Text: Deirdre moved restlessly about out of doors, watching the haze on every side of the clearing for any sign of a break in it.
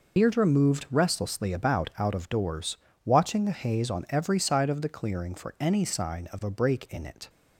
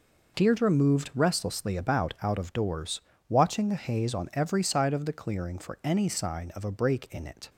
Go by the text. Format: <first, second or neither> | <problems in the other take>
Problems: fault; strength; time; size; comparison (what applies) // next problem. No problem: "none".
second | loses the start of "Deirdre"; at 0.1 s; 55 ms